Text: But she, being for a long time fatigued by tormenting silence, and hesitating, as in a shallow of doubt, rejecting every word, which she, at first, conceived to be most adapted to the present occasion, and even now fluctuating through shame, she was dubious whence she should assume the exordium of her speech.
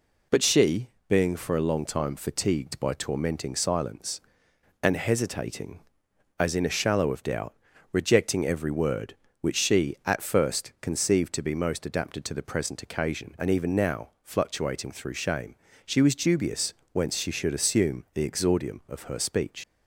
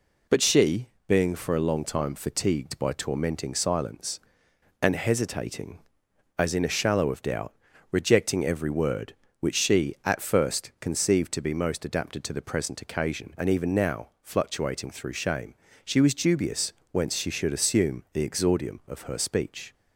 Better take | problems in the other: second | pauses between "dubious" and "whence"; slight; at 16.7 s; 0.18 s long; slight in the second // leaves "speech" unfinished; at 19.6 s; 105 ms

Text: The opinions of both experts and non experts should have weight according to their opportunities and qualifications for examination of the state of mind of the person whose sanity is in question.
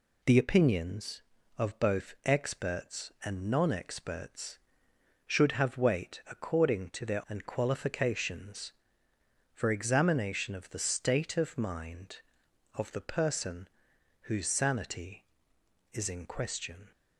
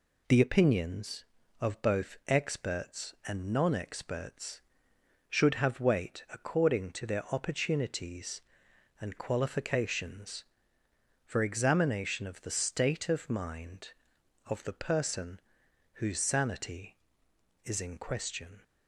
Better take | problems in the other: second | skips "opportunities"; at 7.2 s // pauses between "person" and "whose"; noticeable; at 13.6 s; 0.54 s long; noticeable in the second

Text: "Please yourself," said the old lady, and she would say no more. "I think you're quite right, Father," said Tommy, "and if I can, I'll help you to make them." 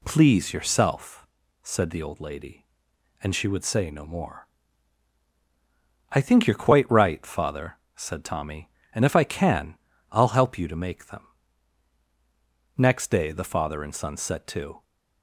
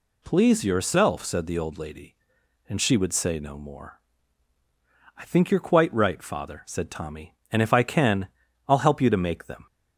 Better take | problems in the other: second | goes on to say "Next day the father and son set to"; strong; from 12.7 s on; 2.0 s long

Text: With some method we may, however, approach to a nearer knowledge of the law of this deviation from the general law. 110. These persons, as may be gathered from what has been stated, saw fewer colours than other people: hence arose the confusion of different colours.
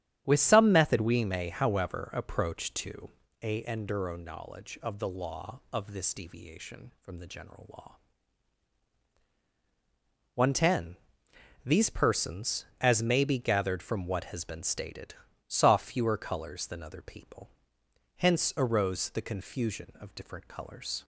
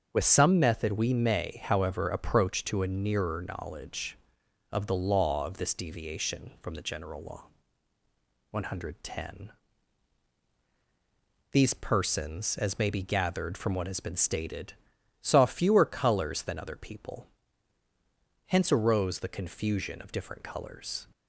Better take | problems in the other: second | starts louder than the rest; strong; until 1.2 s; 10.5 dB; strong in the second // pauses between "to" and "a"; slight; at 3.1 s; 0.32 s long // says "enduro" for "nearer"; at 3.6 s

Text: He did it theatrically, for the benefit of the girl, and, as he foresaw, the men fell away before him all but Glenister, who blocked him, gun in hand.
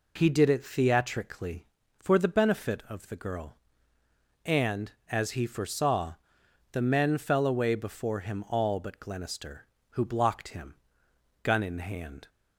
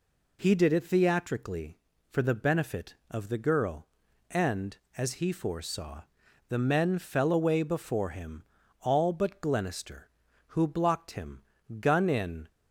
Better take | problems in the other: first | pauses between "him" and "all"; slight; at 8.4 s; 0.36 s long // stops before "hand"; at 12.4 s

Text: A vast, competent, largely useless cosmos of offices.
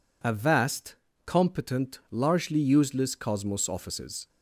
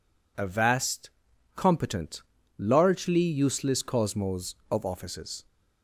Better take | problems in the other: second | skips "of"; at 3.6 s

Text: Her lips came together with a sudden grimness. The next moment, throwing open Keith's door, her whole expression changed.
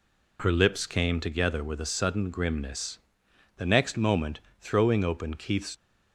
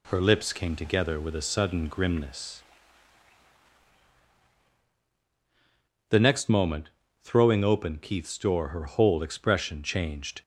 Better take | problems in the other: second | stops before "door her whole expression changed"; at 5.7 s

